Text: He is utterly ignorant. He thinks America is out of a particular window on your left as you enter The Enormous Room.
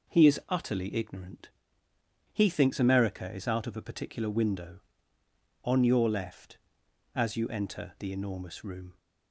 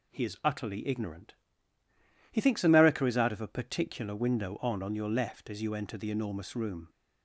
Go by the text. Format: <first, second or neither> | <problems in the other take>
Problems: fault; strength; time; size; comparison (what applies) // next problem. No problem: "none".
first | says "on" twice; at 4.8 s